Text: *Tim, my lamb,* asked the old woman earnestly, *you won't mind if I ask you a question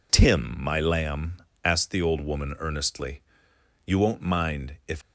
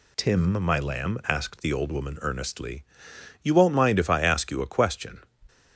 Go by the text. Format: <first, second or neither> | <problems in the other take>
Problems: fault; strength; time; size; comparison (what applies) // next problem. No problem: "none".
second | stops before "I ask you a question"; at 5.0 s